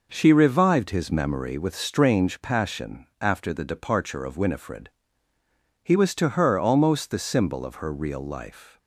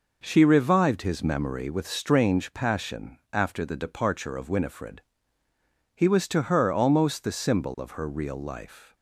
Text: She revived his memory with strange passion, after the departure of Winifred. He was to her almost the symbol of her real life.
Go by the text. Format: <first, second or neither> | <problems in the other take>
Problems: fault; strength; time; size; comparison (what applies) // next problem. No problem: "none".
neither | none